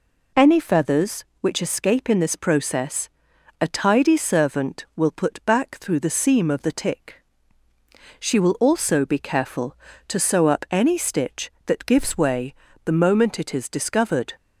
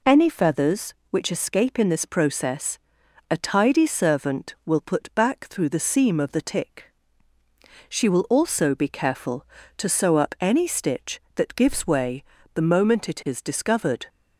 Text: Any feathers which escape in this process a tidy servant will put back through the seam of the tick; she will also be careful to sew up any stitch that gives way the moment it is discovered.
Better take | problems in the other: neither | pauses between "process" and "a"; noticeable; the same in both // pauses between "way" and "the"; slight; the same in both

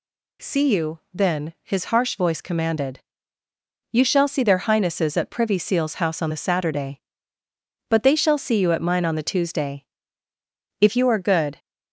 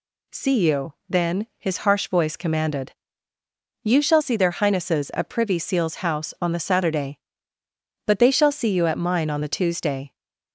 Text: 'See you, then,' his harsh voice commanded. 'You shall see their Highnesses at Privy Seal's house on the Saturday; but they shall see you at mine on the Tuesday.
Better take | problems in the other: second | goes on to say "If you are good"; noticeable; from 10.8 s on; 0.78 s long

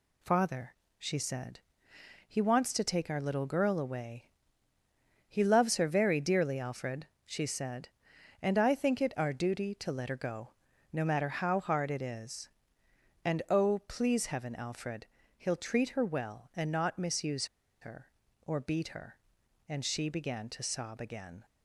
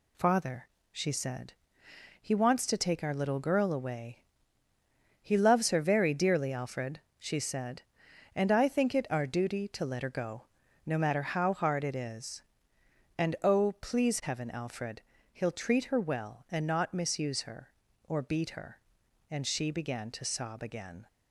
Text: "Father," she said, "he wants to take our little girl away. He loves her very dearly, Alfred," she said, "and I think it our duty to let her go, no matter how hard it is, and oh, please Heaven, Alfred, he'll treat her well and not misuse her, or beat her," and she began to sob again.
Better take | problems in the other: second | pauses between "misuse" and "her"; slight; at 17.4 s; 0.33 s long

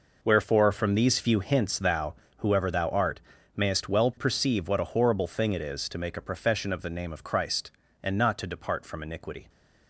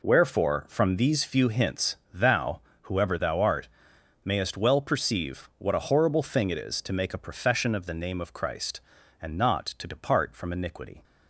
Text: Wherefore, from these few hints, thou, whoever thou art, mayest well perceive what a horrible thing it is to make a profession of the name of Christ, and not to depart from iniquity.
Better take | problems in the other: neither | none

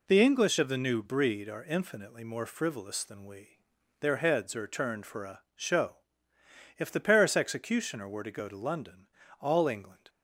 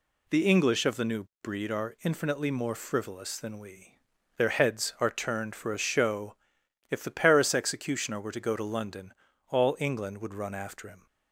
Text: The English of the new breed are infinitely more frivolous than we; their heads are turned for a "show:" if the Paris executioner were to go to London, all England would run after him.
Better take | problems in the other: second | stops before "would run after him"; at 10.0 s

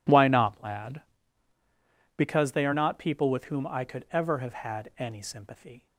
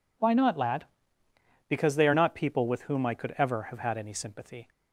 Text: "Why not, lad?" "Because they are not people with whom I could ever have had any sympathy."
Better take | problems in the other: neither | none

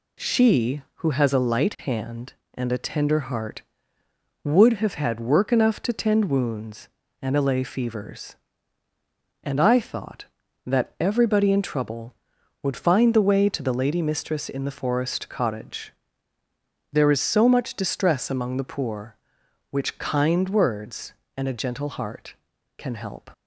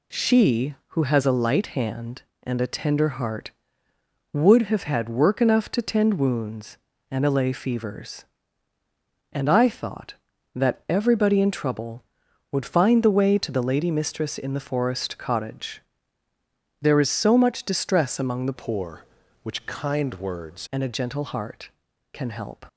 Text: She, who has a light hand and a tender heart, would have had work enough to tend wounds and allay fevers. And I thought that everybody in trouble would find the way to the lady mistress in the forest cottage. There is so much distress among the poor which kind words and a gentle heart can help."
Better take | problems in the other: first | changes voice from "poor" to "words"; from 18.5 to 20.6 s; 2.1 s long

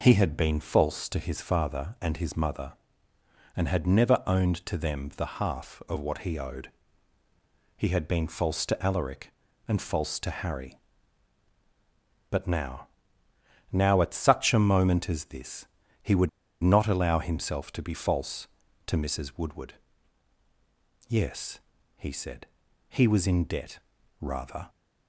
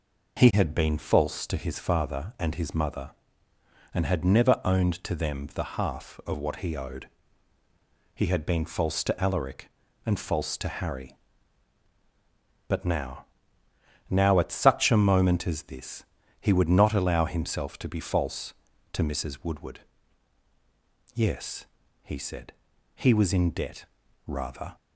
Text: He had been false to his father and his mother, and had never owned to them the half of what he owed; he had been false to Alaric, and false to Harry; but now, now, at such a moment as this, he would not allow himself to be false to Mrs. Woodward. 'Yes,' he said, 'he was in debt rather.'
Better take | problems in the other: second | pauses between "would" and "not"; slight; at 16.2 s; 0.33 s long // pauses between "debt" and "rather"; at 23.7 s; 0.42 s long; also in the second

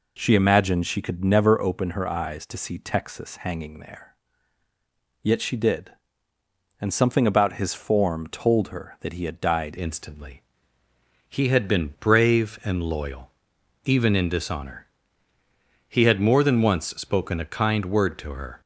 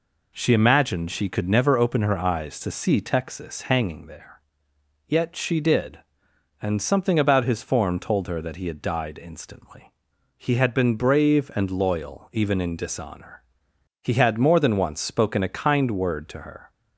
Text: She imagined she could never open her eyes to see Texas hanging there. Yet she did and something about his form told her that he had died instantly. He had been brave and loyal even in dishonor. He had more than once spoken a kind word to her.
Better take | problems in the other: second | changes voice at "instantly"; from 9.7 s on; 8.9 s long // pauses between "loyal" and "even"; noticeable; at 13.3 s; 0.54 s long

